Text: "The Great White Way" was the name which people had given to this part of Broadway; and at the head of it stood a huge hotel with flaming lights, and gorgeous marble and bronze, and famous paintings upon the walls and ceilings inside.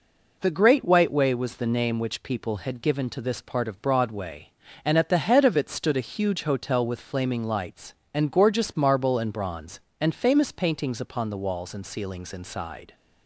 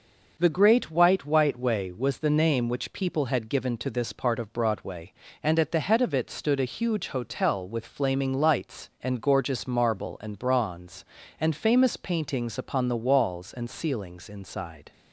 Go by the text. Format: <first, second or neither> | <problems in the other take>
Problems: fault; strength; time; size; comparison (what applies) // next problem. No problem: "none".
first | says "White" twice; at 1.2 s